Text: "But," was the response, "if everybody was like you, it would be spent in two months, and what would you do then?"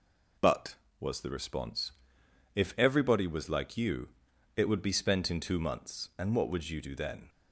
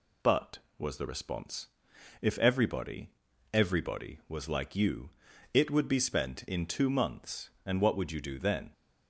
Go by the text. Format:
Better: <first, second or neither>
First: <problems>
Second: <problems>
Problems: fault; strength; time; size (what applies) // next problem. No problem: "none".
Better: first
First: none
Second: says "everybody" twice; at 3.5 s